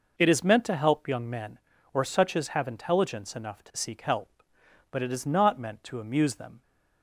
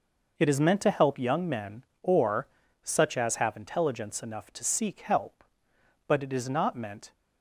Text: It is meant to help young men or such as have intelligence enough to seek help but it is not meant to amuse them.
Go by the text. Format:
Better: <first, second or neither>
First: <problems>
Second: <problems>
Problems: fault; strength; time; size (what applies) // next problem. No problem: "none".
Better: first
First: none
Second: pauses between "or" and "such"; slight; at 2.4 s; 0.34 s long // stops before "to amuse them"; at 7.1 s